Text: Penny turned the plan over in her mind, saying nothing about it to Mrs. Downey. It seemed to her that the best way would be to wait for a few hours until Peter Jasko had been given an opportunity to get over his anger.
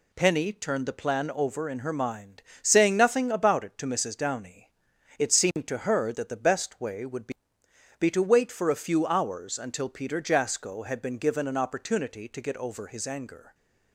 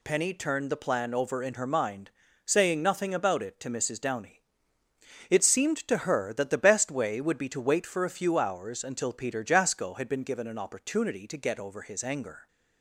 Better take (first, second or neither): second